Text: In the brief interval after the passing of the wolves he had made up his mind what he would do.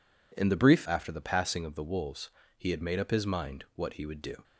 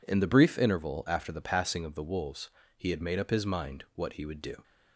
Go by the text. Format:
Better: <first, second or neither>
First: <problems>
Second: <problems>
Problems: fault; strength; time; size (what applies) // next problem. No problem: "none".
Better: second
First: skips "interval"; at 0.8 s // pauses between "wolves" and "he"; slight; at 2.2 s; 0.28 s long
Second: pauses between "wolves" and "he"; slight; at 2.4 s; 0.28 s long